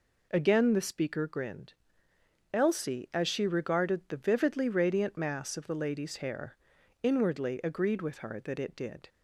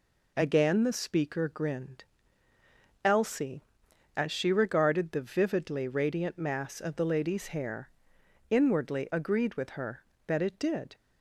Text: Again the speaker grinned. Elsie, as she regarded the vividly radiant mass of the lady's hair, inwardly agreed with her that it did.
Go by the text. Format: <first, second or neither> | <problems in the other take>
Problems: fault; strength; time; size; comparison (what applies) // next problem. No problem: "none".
neither | none